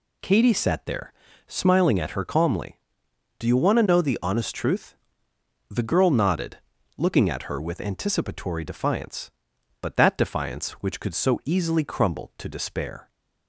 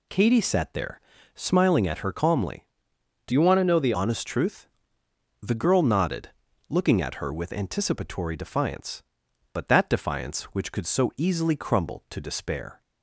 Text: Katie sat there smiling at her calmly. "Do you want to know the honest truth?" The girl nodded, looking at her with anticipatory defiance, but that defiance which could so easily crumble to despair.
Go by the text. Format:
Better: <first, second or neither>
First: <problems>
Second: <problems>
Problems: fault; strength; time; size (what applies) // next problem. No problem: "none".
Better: first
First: pauses between "there" and "smiling"; slight; at 1.1 s; 0.36 s long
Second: pauses between "there" and "smiling"; slight; at 0.9 s; 0.36 s long // changes voice from "you" to "the"; from 3.3 to 3.9 s; 0.6 s long